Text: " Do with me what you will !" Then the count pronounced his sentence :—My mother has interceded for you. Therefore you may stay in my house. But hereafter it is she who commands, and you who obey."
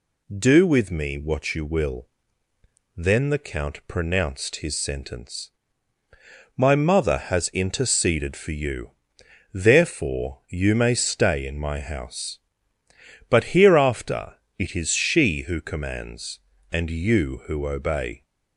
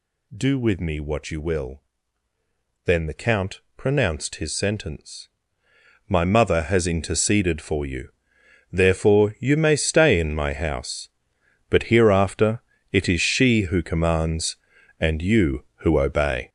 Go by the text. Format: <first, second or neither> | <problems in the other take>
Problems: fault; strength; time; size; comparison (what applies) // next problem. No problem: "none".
first | gets louder; strong; throughout; 14.5 dB // pauses between "count" and "pronounced"; slight; at 3.6 s; 0.16 s long // pauses between "hereafter" and "it"; slight; at 12.6 s; 0.28 s long; slight in the first